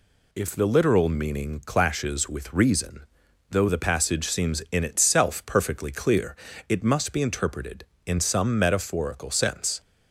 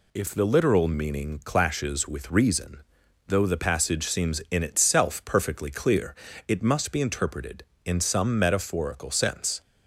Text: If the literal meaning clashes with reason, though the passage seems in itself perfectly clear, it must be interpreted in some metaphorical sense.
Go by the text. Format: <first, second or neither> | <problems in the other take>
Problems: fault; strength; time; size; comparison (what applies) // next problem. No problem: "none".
neither | none